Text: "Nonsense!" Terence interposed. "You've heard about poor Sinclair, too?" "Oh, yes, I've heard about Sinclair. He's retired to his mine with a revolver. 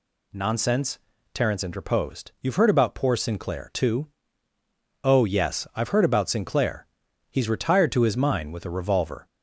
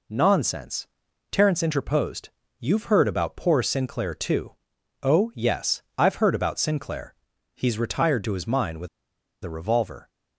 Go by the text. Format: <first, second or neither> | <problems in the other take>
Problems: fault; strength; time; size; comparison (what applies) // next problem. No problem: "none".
first | pauses between "with" and "a"; noticeable; at 8.8 s; 0.56 s long